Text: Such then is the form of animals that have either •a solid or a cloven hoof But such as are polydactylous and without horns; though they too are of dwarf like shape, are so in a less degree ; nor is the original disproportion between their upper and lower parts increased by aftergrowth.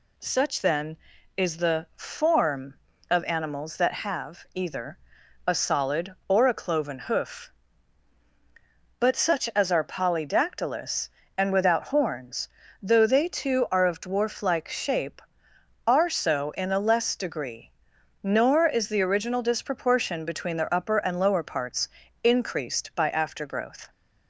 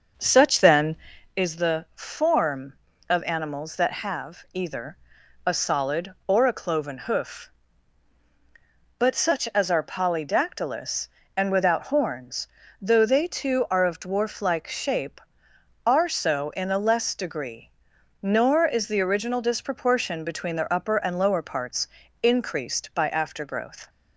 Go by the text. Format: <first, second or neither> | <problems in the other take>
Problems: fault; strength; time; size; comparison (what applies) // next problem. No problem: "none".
first | starts louder than the rest; until 1.4 s; 6.5 dB // pauses between "parts" and "increased"; slight; at 21.8 s; 0.34 s long; slight in the first